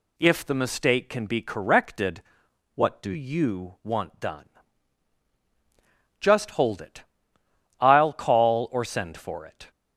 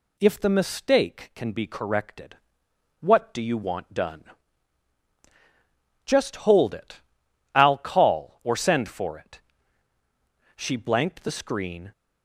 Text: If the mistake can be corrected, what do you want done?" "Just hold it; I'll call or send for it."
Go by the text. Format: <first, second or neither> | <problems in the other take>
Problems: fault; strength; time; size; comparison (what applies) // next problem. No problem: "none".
first | goes on to say "She blanked the screen"; from 10.5 s on; 1.3 s long